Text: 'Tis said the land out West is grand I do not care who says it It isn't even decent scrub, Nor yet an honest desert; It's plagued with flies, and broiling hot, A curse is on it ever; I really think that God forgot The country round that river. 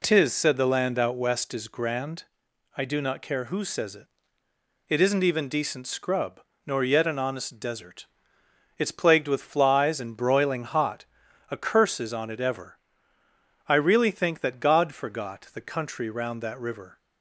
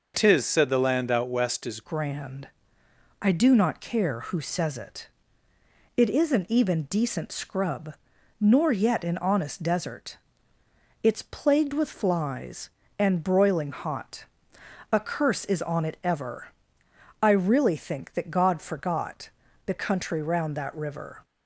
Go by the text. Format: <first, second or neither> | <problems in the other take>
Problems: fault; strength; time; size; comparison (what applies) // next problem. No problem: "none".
first | changes voice at "grand"; from 1.8 s on; 19.4 s long // pauses between "grand" and "I"; noticeable; at 2.4 s; 0.74 s long; noticeable in the first // pauses between "it" and "It"; noticeable; at 5.0 s; 0.88 s long; noticeable in the first // pauses between "forgot" and "The"; slight; at 19.2 s; 0.34 s long